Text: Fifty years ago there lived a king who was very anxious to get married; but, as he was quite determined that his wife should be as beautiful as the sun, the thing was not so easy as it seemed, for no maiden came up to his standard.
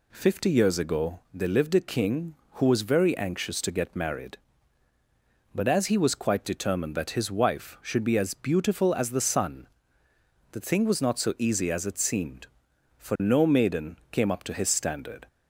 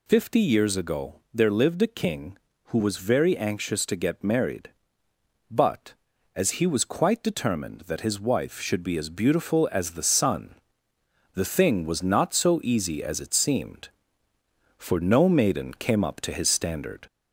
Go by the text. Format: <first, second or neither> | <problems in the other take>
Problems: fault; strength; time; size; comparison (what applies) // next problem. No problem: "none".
first | gets louder; slight; throughout; 2 dB